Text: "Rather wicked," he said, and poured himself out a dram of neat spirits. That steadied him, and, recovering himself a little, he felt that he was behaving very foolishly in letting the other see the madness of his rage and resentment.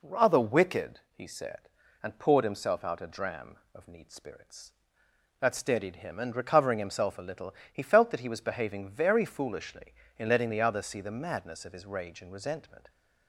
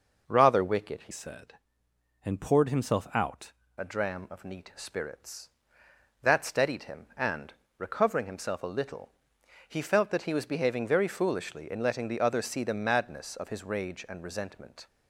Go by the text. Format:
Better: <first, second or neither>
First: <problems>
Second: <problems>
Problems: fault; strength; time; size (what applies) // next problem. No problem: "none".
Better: first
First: none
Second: changes voice from "said" to "out"; from 1.1 to 3.5 s; 2.4 s long